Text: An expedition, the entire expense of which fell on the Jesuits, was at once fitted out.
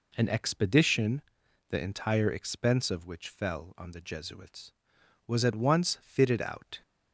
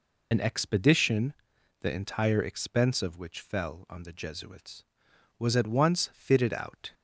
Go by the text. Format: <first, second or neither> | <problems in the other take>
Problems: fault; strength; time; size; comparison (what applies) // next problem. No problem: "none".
first | loses the start of "An"; at 0.3 s; 55 ms